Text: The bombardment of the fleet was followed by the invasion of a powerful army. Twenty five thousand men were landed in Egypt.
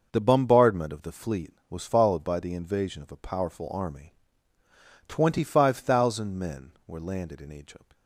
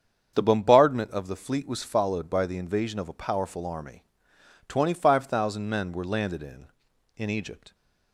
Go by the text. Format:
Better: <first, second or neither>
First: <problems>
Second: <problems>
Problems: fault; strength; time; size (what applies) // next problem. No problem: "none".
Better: first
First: starts louder than the rest; noticeable; until 1.1 s; 6 dB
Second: starts louder than the rest; strong; until 1.3 s; 7.5 dB // says "in" twice; at 7.1 s